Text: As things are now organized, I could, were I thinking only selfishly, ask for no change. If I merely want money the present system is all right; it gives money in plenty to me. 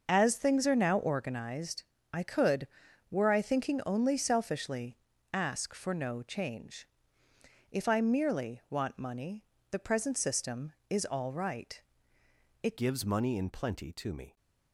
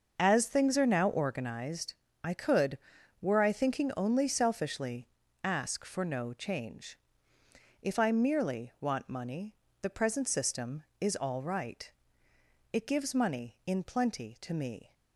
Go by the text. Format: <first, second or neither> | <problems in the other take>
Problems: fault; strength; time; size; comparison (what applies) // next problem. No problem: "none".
second | starts louder than the rest; until 1.1 s; 6 dB; also in the second // pauses between "money" and "the"; slight; at 9.4 s; 0.28 s long; slight in the second // changes voice at "gives"; from 12.7 s on; 1.6 s long